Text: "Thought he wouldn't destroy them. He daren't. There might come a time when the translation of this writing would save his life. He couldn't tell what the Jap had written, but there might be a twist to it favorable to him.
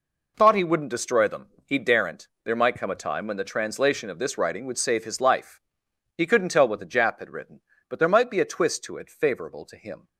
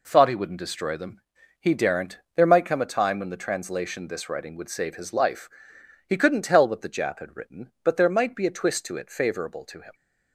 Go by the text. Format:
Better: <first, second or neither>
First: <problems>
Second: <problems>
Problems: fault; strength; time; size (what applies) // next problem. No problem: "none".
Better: first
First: none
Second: skips "of"; at 4.0 s